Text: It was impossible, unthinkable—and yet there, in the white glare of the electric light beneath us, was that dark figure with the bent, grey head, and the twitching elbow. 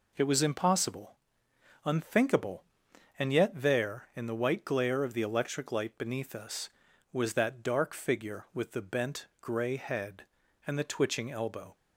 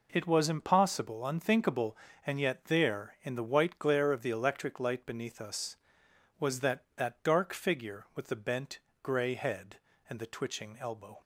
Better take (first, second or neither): first